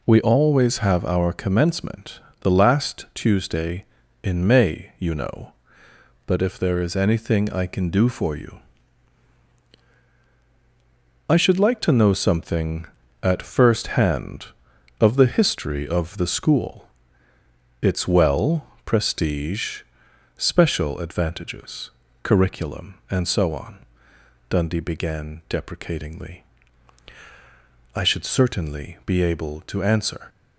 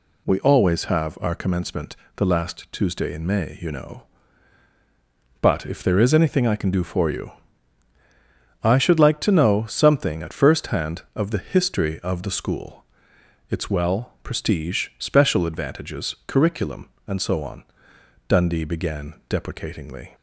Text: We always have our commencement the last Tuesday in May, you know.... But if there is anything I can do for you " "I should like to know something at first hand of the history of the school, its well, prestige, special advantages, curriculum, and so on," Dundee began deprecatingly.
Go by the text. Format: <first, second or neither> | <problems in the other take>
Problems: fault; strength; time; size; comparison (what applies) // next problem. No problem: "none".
second | pauses between "commencement" and "the"; slight; at 2.1 s; 0.22 s long; slight in the second // goes on to say "I should certainly be able to answer"; strong; from 27.9 s on; 2.3 s long